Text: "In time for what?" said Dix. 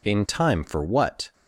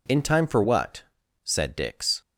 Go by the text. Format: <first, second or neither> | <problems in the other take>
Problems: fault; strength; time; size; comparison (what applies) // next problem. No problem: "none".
second | stops before "said Dix"; at 1.3 s